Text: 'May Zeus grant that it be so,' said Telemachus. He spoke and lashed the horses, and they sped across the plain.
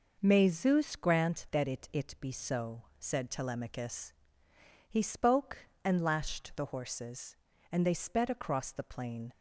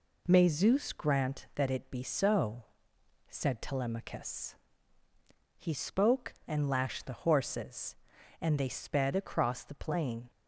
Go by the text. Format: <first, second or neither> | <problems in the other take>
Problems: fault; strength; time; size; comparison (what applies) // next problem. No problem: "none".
second | says "it" twice; at 1.9 s